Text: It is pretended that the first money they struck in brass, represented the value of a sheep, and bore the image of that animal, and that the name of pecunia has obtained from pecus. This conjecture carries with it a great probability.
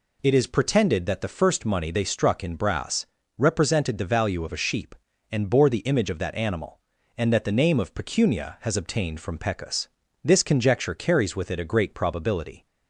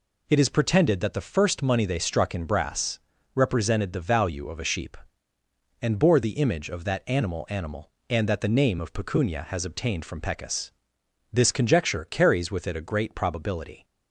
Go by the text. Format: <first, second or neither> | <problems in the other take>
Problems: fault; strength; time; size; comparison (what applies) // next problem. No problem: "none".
first | says "animal" twice; at 7.5 s